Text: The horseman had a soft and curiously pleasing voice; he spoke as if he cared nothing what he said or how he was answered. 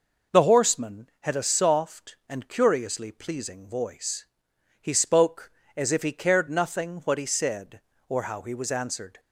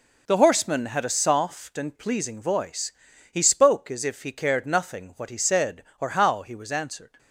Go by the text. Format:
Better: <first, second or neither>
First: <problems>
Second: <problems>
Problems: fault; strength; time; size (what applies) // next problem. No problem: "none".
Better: first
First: none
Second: skips "curiously"; at 1.9 s